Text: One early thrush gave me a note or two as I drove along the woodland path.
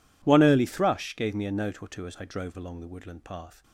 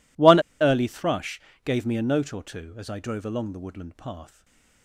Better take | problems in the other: first | pauses between "One" and "early"; slight; at 0.3 s; 0.20 s long // pauses between "thrush" and "gave"; slight; at 1.4 s; 0.22 s long // stays silent after the last word; slight; from 4.2 s on; 0.6 s long

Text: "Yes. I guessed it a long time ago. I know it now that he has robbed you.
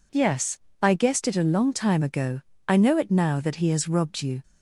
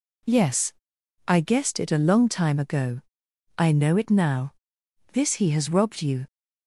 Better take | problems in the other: first | says "this" for "that"; at 5.1 s

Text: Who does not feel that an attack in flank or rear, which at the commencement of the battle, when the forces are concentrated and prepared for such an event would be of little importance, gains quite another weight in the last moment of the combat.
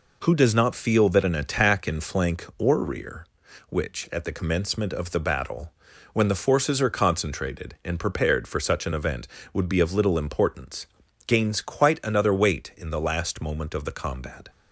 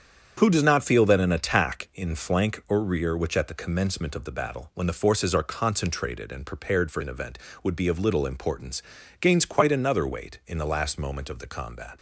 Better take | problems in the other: first | starts louder than the rest; strong; until 1.4 s; 8 dB // skips "such"; at 7.0 s

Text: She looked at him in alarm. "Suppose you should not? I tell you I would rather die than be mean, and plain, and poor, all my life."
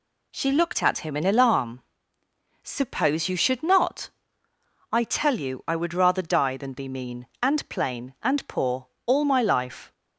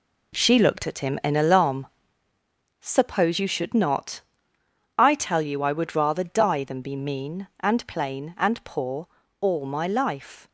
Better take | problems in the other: first | gets quieter; strong; throughout; 8 dB

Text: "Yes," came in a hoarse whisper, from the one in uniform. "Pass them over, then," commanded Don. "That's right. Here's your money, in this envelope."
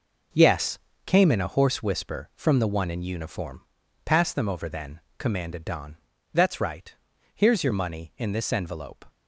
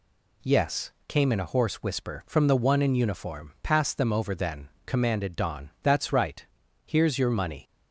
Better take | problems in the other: first | stops before "in this envelope"; at 7.6 s

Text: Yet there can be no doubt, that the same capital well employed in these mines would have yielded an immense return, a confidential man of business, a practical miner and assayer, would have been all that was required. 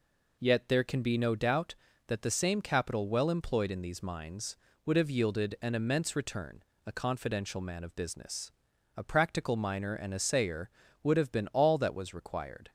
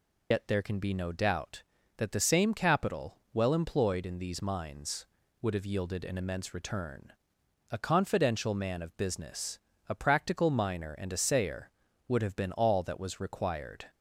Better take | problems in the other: first | loses the start of "Yet"; at 0.3 s; 85 ms // pauses between "capital" and "well"; slight; at 3.1 s; 0.16 s long

